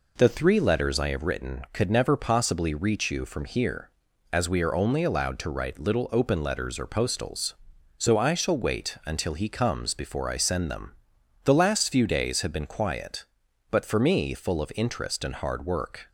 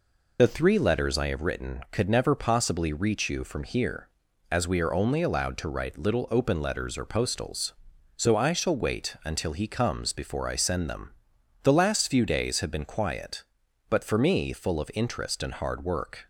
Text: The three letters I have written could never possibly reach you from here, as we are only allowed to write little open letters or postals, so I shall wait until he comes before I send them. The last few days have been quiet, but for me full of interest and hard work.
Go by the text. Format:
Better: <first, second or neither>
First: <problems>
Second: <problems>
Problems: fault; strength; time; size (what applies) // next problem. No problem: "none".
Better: first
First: none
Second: loses the start of "The"; at 0.3 s; 45 ms